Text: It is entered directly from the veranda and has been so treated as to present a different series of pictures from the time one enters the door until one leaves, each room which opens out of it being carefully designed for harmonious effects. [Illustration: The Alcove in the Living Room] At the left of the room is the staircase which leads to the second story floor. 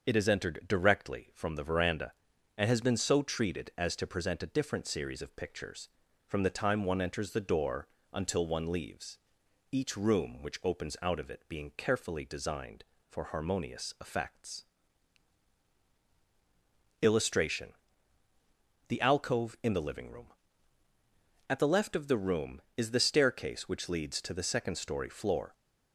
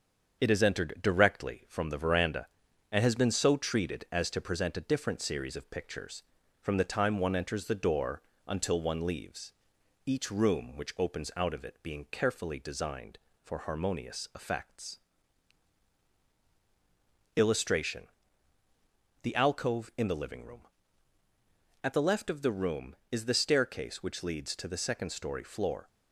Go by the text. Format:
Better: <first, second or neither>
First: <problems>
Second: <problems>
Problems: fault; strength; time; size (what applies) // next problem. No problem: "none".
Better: first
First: starts louder than the rest; until 1.1 s; 6.5 dB // pauses between "door" and "until"; slight; at 7.8 s; 0.26 s long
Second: gets quieter; slight; throughout; 3 dB // starts louder than the rest; strong; until 1.4 s; 7 dB // pauses between "door" and "until"; slight; at 8.2 s; 0.26 s long